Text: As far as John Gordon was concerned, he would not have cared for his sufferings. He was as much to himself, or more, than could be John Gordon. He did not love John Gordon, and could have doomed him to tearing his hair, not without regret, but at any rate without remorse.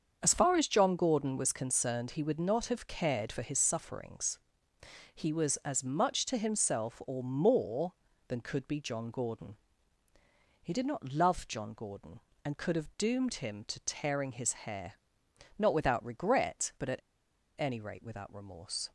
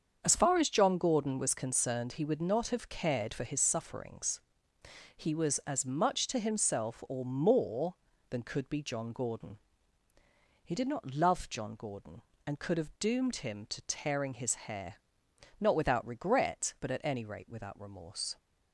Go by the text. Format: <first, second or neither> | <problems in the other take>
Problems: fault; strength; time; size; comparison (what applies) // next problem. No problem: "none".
second | starts louder than the rest; strong; until 1.2 s; 7 dB; strong in the second // pauses between "at" and "any"; noticeable; at 16.9 s; 0.59 s long